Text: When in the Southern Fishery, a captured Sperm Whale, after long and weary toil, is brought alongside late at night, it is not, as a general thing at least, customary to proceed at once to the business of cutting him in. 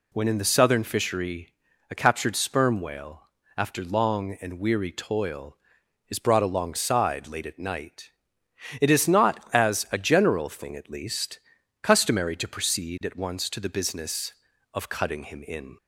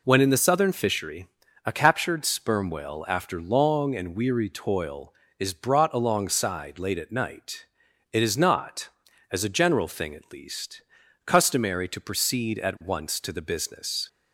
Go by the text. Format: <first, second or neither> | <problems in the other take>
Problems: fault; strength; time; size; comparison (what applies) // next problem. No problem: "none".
first | stops before "of cutting him in"; at 14.0 s